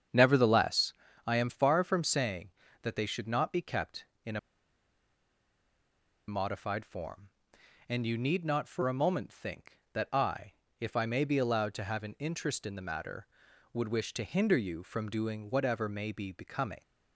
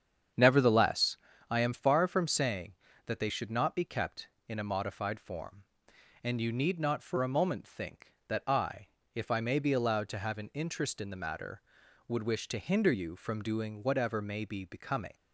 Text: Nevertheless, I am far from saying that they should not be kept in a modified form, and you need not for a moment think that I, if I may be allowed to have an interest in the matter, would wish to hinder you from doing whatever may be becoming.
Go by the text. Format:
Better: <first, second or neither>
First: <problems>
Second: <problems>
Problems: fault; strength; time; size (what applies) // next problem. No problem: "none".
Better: second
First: starts louder than the rest; strong; until 1.4 s; 8 dB // pauses between "a" and "modified"; strong; at 4.3 s; 1.9 s long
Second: starts louder than the rest; strong; until 1.6 s; 8 dB